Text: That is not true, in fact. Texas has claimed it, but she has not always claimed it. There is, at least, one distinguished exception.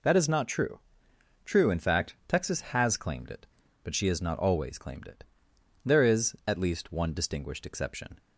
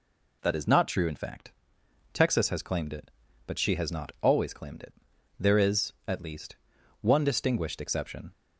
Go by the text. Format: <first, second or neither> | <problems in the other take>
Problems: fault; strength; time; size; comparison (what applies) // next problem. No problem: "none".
second | says "true" twice; at 1.4 s